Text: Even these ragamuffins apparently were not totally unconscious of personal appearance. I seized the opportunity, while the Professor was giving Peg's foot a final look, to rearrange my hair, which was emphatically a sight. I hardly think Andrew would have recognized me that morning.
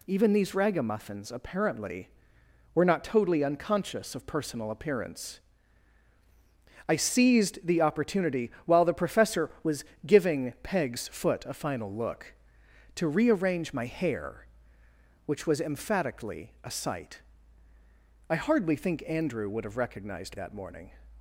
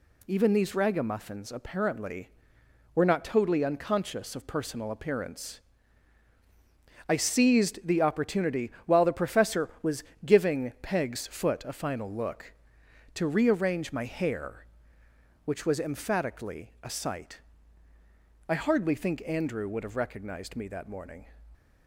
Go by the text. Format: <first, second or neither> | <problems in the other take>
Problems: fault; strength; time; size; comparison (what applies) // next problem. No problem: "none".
second | pauses between "was" and "giving"; slight; at 9.8 s; 0.22 s long; slight in the second // skips "me"; at 20.3 s